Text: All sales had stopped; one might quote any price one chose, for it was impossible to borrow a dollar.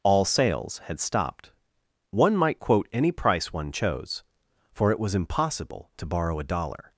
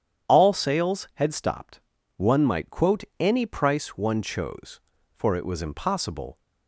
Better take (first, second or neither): first